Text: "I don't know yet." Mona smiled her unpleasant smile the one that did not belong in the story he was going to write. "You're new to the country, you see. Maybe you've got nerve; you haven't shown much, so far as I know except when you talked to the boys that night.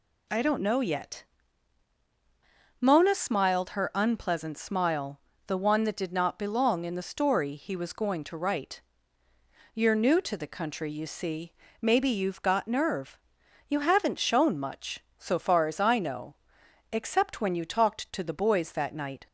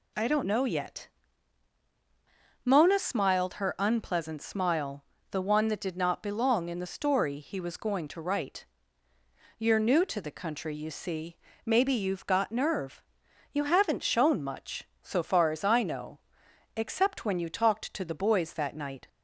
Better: neither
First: pauses between "smile" and "the"; slight; at 5.1 s; 0.26 s long // pauses between "know" and "except"; noticeable; at 16.3 s; 0.56 s long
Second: pauses between "smile" and "the"; slight; at 5.0 s; 0.26 s long // pauses between "know" and "except"; noticeable; at 16.1 s; 0.56 s long

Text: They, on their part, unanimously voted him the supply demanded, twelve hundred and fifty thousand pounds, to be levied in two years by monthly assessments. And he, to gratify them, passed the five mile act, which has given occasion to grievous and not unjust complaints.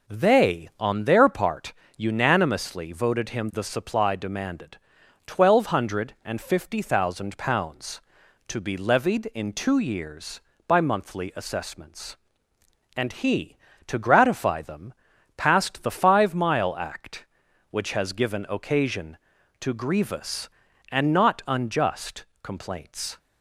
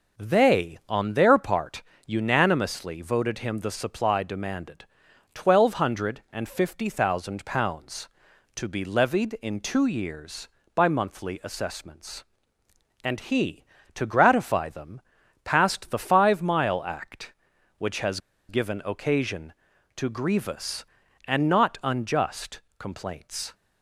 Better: first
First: pauses between "unjust" and "complaints"; slight; at 22.2 s; 0.18 s long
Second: pauses between "has" and "given"; slight; at 18.1 s; 0.29 s long // pauses between "unjust" and "complaints"; slight; at 22.6 s; 0.18 s long

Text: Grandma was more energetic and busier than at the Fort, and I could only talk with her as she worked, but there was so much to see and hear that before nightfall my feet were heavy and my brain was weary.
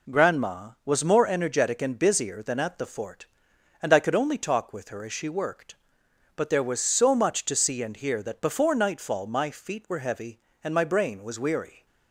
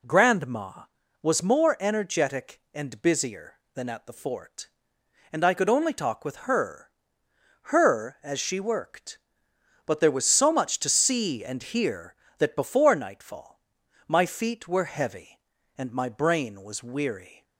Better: first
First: none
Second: says "her" twice; at 7.6 s // pauses between "nightfall" and "my"; noticeable; at 13.5 s; 0.48 s long

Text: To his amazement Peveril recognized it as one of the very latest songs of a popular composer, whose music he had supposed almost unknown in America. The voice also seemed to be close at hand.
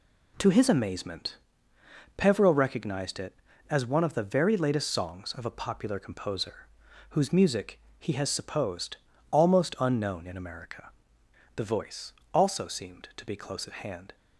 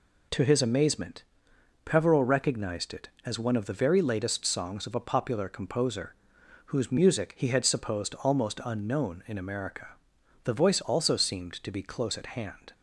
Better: second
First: pauses between "amazement" and "Peveril"; noticeable; at 1.3 s; 0.80 s long // pauses between "music" and "he"; slight; at 7.7 s; 0.20 s long // says "has" for "had"; at 8.1 s // pauses between "supposed" and "almost"; slight; at 8.9 s; 0.34 s long // pauses between "voice" and "also"; slight; at 12.1 s; 0.20 s long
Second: pauses between "amazement" and "Peveril"; noticeable; at 1.2 s; 0.62 s long

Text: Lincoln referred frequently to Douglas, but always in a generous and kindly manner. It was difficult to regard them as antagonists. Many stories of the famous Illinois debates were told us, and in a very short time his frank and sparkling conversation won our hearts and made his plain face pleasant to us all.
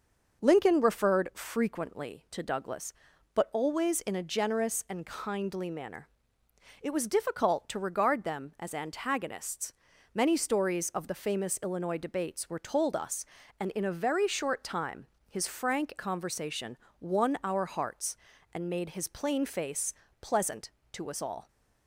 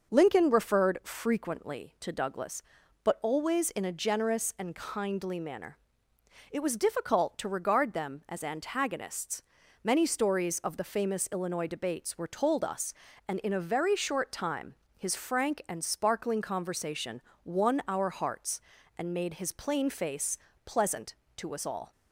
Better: second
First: starts louder than the rest; until 1.4 s; 6 dB // pauses between "time" and "his"; slight; at 15.0 s; 0.20 s long // skips "and sparkling"; at 15.9 s // pauses between "conversation" and "won"; slight; at 16.7 s; 0.24 s long // pauses between "face" and "pleasant"; slight; at 19.9 s; 0.26 s long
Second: starts louder than the rest; until 1.1 s; 6 dB // pauses between "time" and "his"; slight; at 14.7 s; 0.20 s long // pauses between "conversation" and "won"; slight; at 17.1 s; 0.24 s long // pauses between "face" and "pleasant"; slight; at 20.3 s; 0.26 s long

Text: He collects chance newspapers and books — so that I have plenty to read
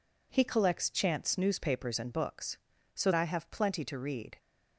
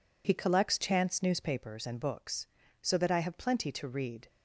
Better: second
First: skips "that"; at 3.1 s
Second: none

